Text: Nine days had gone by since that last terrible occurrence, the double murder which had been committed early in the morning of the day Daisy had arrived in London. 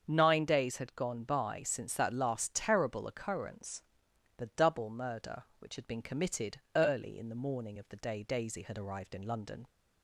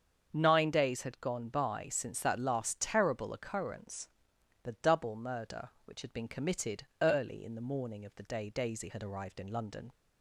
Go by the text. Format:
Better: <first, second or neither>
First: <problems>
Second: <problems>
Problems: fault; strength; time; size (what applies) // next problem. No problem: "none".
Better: neither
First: starts louder than the rest; until 1.0 s; 7 dB // pauses between "committed" and "early"; slight; at 6.5 s; 0.18 s long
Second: starts louder than the rest; until 1.3 s; 7 dB // pauses between "committed" and "early"; slight; at 6.8 s; 0.18 s long